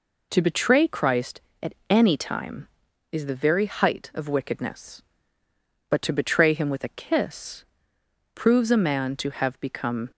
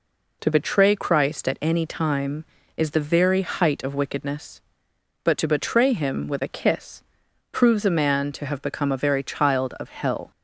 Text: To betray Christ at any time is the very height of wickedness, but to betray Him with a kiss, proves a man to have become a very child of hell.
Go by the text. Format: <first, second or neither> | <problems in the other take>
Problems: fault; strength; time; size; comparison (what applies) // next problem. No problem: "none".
second | stops before "a very child of hell"; at 10.1 s